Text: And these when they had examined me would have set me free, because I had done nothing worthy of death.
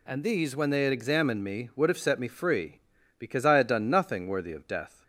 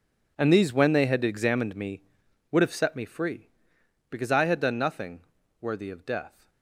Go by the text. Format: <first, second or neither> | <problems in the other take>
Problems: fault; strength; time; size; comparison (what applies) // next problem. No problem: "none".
first | gets quieter; strong; throughout; 16.5 dB // pauses between "nothing" and "worthy"; at 5.2 s; 0.40 s long